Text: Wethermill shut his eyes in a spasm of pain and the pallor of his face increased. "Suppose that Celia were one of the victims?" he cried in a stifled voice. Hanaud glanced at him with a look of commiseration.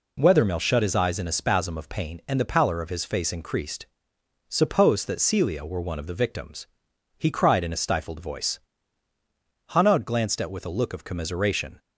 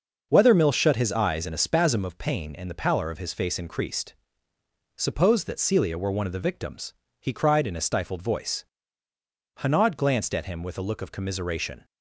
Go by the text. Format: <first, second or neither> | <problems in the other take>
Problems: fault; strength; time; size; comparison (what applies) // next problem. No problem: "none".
second | skips "him"; at 10.5 s